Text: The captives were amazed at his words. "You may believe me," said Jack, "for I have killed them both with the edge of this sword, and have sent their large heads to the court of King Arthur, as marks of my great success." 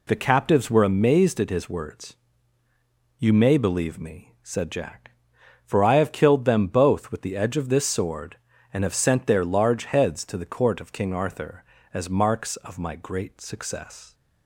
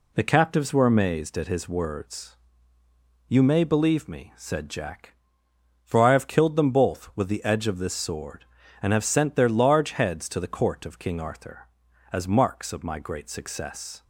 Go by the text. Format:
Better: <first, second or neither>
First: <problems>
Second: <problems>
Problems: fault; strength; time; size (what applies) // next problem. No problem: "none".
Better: neither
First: none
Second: none